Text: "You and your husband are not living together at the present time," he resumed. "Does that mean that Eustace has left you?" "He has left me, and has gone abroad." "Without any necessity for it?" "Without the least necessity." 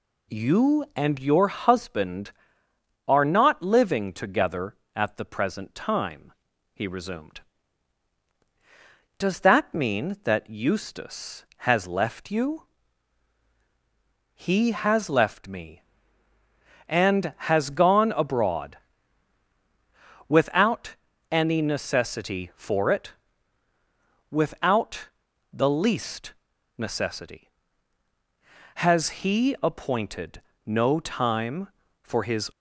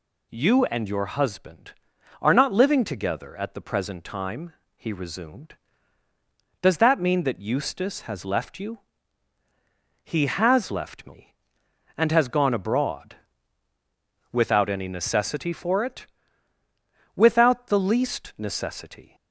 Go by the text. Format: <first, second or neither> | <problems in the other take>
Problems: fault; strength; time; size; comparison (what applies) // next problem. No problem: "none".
second | pauses between "Without" and "any"; slight; at 20.9 s; 0.36 s long // pauses between "Without" and "the"; at 25.0 s; 0.44 s long // pauses between "least" and "necessity"; at 26.3 s; 0.42 s long // goes on to say "Has he appointed no time for his"; strong; from 28.7 s on; 3.7 s long